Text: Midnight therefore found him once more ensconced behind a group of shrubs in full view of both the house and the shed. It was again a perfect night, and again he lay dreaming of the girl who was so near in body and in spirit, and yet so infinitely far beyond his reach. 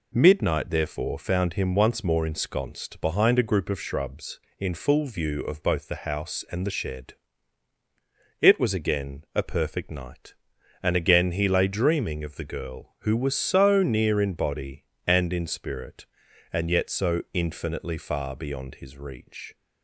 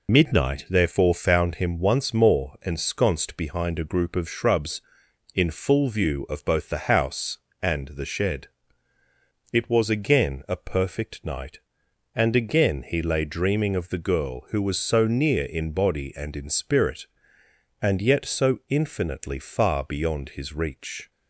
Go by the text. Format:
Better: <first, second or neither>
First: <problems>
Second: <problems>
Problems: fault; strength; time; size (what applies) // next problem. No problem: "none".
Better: first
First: none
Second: loses the start of "Midnight"; at 0.0 s; 80 ms